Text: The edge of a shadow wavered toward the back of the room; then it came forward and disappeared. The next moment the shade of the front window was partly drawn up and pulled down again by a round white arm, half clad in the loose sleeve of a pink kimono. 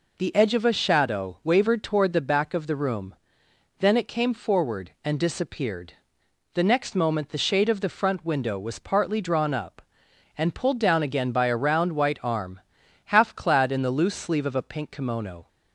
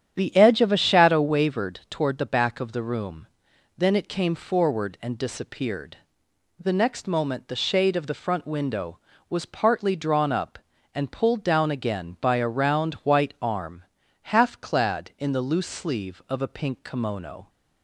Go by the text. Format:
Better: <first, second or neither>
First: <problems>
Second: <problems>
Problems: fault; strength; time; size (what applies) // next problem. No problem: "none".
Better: first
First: none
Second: starts louder than the rest; strong; until 1.4 s; 9 dB